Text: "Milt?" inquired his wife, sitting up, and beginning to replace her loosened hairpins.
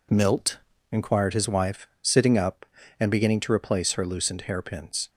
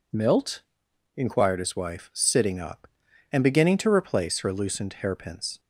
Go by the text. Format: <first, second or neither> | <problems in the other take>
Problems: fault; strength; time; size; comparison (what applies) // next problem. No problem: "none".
neither | none